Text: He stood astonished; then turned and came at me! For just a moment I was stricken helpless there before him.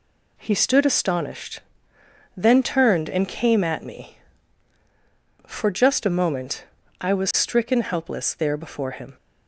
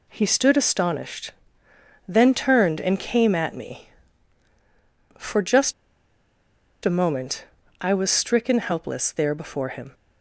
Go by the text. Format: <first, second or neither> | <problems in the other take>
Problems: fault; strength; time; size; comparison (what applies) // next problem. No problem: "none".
first | pauses between "just" and "a"; at 5.7 s; 1.1 s long // pauses between "moment" and "I"; slight; at 7.4 s; 0.36 s long; slight in the first